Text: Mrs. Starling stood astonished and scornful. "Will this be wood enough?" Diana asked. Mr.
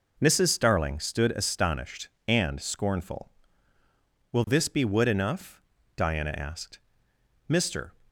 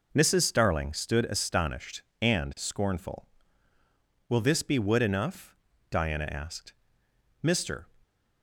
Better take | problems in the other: neither | none

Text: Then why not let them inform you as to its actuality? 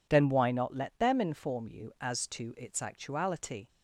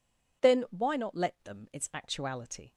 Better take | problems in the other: first | skips "inform you as to"; at 1.7 s

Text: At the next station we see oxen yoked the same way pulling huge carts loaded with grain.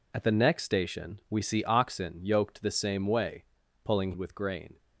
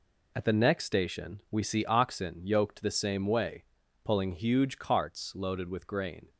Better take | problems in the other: second | pauses between "way" and "pulling"; at 3.4 s; 0.40 s long; also in the second // skips "huge carts loaded"; at 4.1 s

